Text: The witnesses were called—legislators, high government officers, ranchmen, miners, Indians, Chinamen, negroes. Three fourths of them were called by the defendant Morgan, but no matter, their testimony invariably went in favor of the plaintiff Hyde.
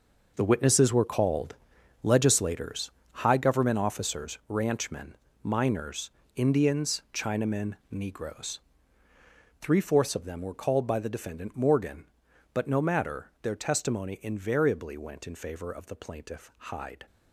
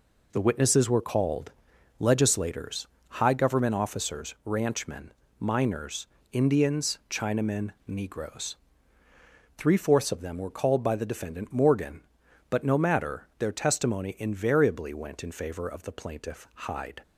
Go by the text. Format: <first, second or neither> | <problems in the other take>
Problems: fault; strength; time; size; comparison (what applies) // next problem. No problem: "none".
second | gets quieter; strong; throughout; 11.5 dB